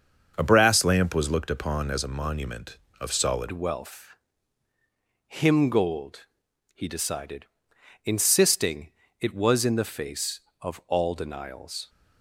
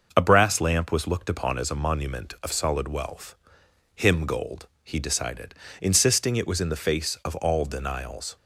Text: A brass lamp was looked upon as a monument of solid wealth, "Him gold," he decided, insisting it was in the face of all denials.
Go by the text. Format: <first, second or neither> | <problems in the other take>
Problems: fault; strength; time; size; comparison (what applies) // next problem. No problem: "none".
second | starts louder than the rest; until 1.3 s; 6.5 dB // changes voice at "wealth"; from 3.5 s on; 8.3 s long // pauses between "insisting" and "it"; slight; at 8.9 s; 0.26 s long